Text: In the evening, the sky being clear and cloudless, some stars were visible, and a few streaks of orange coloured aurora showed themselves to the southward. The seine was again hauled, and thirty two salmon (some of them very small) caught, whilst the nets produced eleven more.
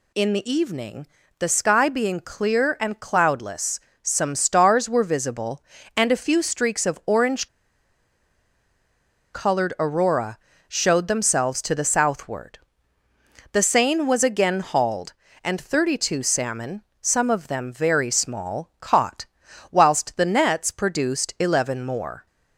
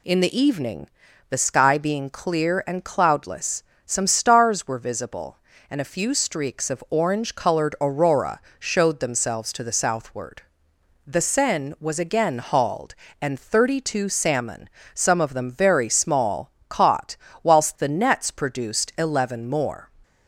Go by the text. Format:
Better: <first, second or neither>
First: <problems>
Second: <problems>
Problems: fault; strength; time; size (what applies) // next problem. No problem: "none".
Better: second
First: pauses between "orange" and "coloured"; strong; at 7.4 s; 1.8 s long // pauses between "aurora" and "showed"; slight; at 10.3 s; 0.30 s long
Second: pauses between "aurora" and "showed"; slight; at 8.4 s; 0.18 s long